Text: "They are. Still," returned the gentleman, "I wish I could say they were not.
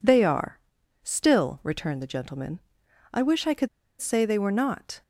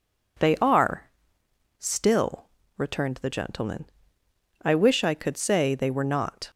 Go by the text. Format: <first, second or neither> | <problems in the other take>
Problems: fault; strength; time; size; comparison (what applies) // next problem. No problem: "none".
second | pauses between "could" and "say"; slight; at 3.6 s; 0.31 s long